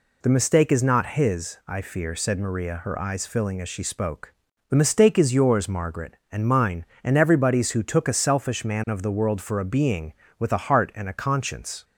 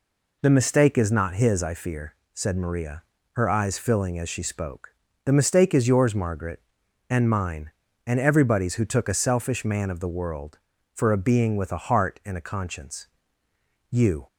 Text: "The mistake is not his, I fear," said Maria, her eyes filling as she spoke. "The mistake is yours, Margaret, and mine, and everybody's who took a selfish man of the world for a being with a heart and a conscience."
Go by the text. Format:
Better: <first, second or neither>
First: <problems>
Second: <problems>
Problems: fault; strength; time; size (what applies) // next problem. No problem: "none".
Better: first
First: none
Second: goes on to say "You"; slight; from 13.8 s on; 0.38 s long